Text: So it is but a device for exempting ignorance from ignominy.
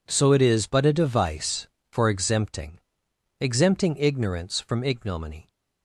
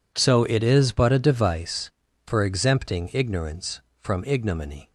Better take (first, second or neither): second